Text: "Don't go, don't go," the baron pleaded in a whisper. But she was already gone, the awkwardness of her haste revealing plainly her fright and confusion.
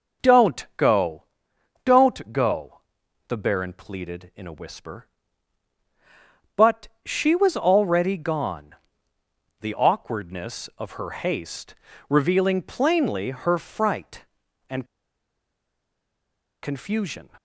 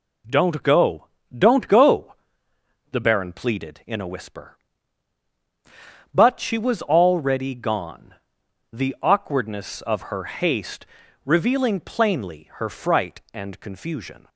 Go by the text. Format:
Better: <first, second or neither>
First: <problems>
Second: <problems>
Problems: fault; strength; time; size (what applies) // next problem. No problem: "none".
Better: second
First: pauses between "But" and "she"; slight; at 6.8 s; 0.18 s long // pauses between "haste" and "revealing"; slight; at 11.7 s; 0.34 s long // pauses between "and" and "confusion"; strong; at 14.8 s; 1.7 s long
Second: pauses between "haste" and "revealing"; at 10.8 s; 0.40 s long